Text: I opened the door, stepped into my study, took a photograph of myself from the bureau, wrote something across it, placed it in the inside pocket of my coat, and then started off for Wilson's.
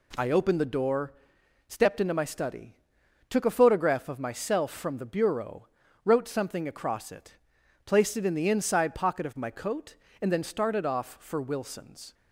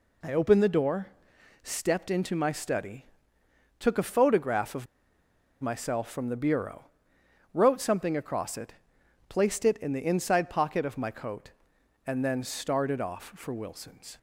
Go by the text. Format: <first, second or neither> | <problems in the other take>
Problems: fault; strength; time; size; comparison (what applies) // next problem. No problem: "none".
first | pauses between "of" and "myself"; noticeable; at 4.8 s; 0.75 s long